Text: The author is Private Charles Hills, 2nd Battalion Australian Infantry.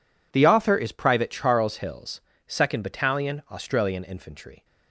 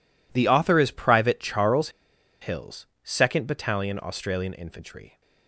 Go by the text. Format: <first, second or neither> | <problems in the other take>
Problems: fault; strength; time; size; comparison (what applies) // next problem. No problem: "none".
first | pauses between "Charles" and "Hills"; noticeable; at 1.8 s; 0.52 s long